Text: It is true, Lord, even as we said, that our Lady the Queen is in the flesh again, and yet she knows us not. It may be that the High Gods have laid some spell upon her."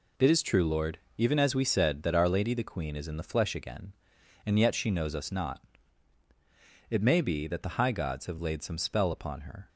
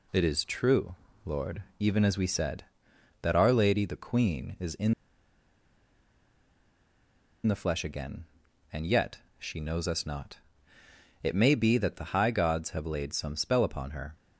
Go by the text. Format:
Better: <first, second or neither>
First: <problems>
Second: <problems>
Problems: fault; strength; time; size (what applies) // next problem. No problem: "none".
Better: first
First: none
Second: pauses between "in" and "the"; strong; at 4.9 s; 2.5 s long // pauses between "yet" and "she"; slight; at 9.1 s; 0.18 s long